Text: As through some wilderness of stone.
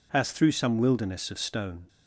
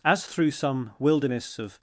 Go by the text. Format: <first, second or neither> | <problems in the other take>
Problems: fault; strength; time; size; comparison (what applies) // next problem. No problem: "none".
first | stops before "stone"; at 1.7 s